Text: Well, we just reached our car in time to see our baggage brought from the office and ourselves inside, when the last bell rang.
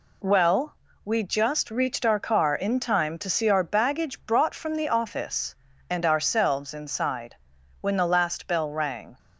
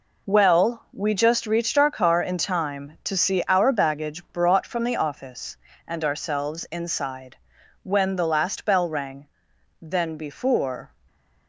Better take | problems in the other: first | goes on to say "Then before"; noticeable; from 9.8 s on; 1.0 s long

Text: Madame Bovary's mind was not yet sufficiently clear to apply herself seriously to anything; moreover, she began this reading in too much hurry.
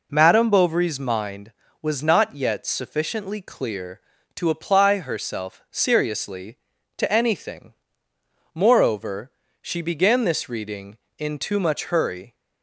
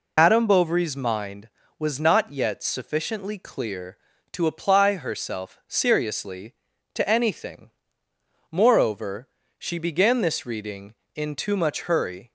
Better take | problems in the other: first | loses the start of "Madame"; at 0.1 s; 100 ms

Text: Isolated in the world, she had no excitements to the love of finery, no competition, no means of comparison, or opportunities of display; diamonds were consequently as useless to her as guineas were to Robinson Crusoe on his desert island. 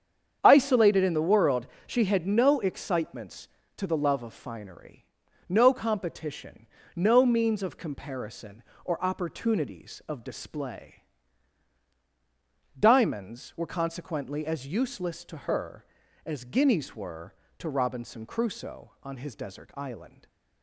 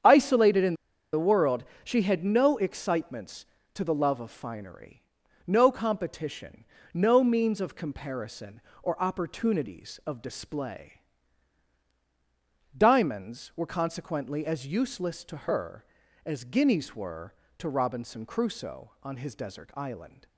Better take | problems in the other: first | starts louder than the rest; strong; until 1.4 s; 8 dB; strong in the first // pauses between "in" and "the"; at 0.7 s; 0.38 s long

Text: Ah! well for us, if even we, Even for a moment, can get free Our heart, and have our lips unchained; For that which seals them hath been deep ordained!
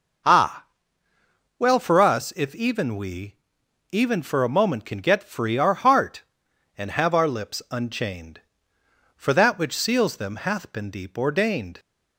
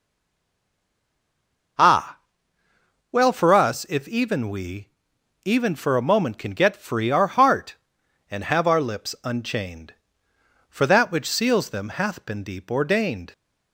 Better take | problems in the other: first | stays silent before the first word; noticeable; until 1.7 s; 1.7 s long // starts louder than the rest; noticeable; until 3.7 s; 6 dB; noticeable in the first

